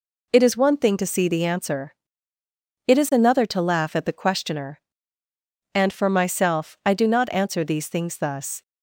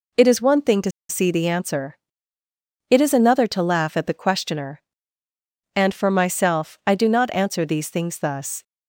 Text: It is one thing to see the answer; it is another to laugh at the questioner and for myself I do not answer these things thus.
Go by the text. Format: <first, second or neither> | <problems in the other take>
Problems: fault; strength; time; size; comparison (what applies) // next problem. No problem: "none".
first | pauses between "to" and "see"; slight; at 0.9 s; 0.18 s long